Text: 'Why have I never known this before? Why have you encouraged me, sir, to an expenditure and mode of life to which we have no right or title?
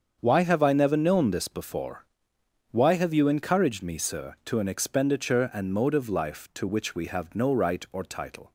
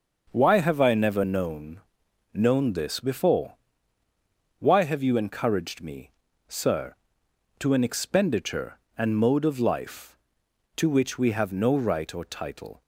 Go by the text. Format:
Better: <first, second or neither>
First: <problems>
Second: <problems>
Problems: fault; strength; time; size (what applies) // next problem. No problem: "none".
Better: first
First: starts louder than the rest; until 1.2 s; 7 dB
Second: starts louder than the rest; until 1.3 s; 6 dB // says "known" twice; at 2.3 s